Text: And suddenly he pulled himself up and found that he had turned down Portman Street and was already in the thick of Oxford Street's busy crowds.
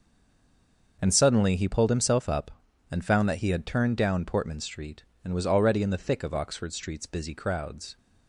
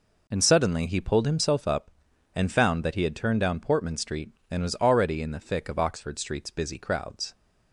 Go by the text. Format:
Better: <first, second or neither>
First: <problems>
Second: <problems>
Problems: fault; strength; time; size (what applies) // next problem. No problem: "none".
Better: second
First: stays silent before the first word; until 0.9 s; 0.9 s long // starts louder than the rest; until 2.0 s; 6 dB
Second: none